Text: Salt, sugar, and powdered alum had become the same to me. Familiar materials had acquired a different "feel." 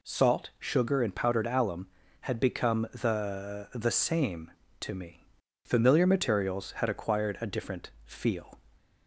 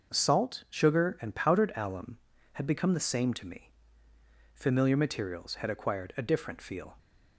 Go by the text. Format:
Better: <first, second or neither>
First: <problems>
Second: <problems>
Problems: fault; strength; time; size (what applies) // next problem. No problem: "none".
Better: second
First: says "the" twice; at 3.7 s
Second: none